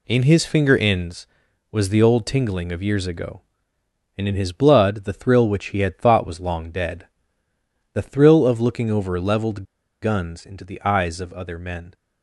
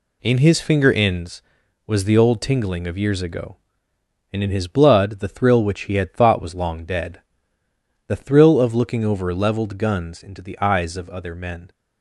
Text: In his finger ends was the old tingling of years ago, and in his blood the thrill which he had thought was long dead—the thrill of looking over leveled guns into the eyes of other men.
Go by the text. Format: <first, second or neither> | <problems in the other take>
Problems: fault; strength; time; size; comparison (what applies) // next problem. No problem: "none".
second | pauses between "leveled" and "guns"; at 9.6 s; 0.39 s long